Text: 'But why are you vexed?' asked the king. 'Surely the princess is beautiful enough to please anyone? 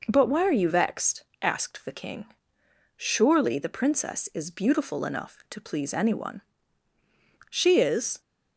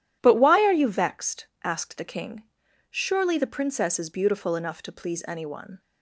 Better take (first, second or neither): second